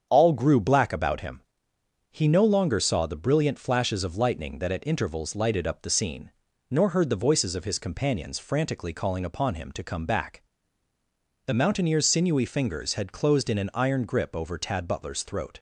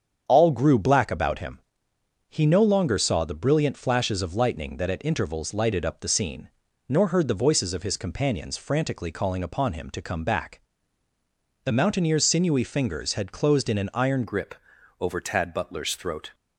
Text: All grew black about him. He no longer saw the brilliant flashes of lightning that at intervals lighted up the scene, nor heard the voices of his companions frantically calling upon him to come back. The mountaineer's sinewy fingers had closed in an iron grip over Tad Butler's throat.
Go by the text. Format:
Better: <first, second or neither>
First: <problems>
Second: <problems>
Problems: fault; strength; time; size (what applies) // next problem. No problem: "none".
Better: first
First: starts louder than the rest; strong; until 1.1 s; 7.5 dB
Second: starts louder than the rest; strong; until 1.2 s; 7.5 dB // changes voice at "grip"; from 14.2 s on; 2.1 s long // pauses between "grip" and "over"; noticeable; at 14.5 s; 0.46 s long